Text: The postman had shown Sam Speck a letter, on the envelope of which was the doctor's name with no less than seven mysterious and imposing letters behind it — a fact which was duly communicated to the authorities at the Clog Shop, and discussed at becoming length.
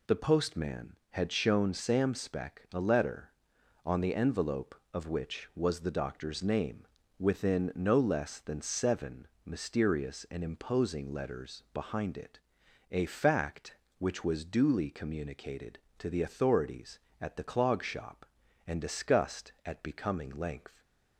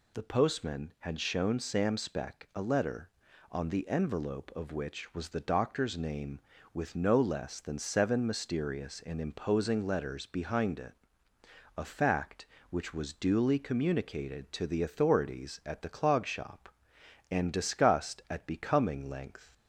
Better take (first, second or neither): second